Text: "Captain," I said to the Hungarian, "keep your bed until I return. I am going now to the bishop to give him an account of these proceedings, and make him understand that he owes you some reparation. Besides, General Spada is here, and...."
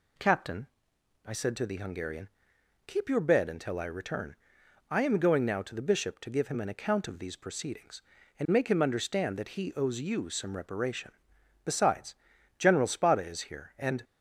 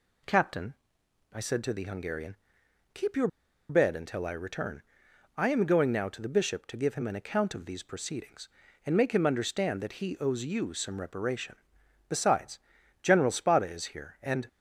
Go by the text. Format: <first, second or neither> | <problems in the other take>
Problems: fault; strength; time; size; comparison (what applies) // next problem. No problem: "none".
first | pauses between "your" and "bed"; at 3.2 s; 0.42 s long